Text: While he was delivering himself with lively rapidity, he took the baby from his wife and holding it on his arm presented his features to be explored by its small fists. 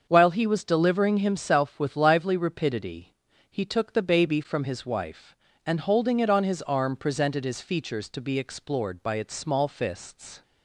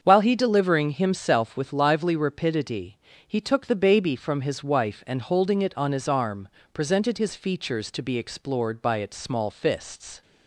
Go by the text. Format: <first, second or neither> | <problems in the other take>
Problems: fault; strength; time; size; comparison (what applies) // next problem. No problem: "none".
first | starts louder than the rest; until 1.0 s; 7 dB; also in the first // skips "was"; at 0.3 s // pauses between "arm" and "presented"; slight; at 6.4 s; 0.26 s long